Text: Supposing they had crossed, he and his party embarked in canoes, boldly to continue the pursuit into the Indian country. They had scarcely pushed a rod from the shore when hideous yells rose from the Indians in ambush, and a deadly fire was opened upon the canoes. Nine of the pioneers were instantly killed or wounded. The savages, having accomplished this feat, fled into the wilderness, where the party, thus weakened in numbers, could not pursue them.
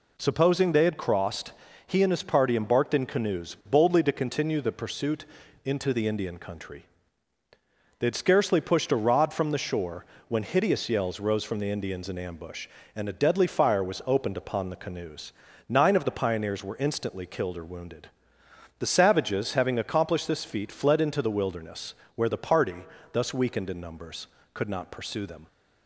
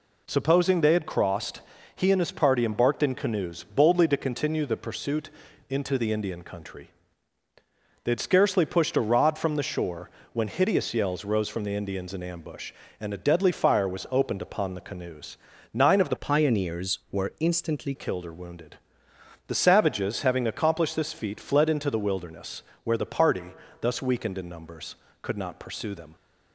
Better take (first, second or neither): first